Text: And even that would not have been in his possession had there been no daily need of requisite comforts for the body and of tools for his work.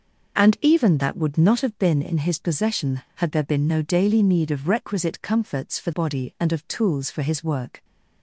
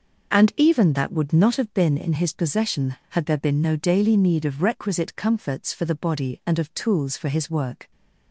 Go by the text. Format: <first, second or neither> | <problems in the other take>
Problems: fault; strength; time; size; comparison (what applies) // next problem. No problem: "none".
second | skips "the"; at 5.9 s